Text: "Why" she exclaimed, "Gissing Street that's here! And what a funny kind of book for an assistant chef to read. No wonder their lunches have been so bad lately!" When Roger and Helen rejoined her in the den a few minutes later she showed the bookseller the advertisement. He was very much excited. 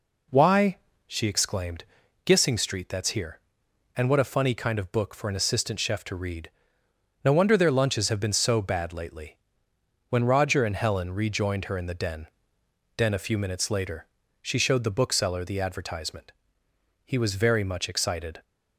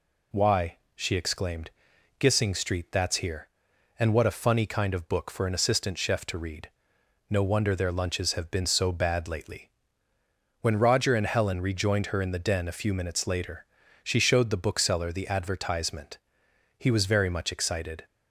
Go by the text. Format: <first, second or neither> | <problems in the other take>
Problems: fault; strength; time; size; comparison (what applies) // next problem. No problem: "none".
second | pauses between "Why" and "she"; slight; at 0.7 s; 0.30 s long; slight in the second // says "den" twice; at 12.9 s // pauses between "later" and "she"; slight; at 14.0 s; 0.36 s long; also in the second